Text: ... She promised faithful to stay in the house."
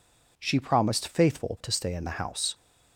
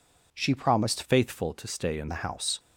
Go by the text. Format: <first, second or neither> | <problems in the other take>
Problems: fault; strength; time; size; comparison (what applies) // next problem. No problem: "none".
first | changes voice from "faithful" to "in"; from 1.0 to 2.0 s; 1.0 s long